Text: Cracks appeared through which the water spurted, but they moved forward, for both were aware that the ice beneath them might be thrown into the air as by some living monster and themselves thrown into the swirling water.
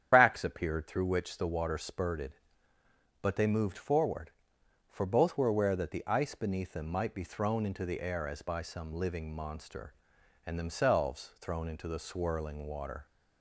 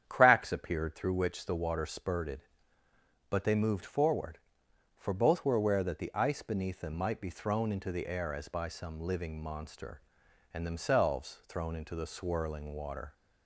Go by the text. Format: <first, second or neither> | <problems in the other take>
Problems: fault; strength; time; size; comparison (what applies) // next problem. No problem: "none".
second | loses the start of "Cracks"; at 0.1 s; 140 ms // starts louder than the rest; strong; until 1.1 s; 9 dB; strong in the second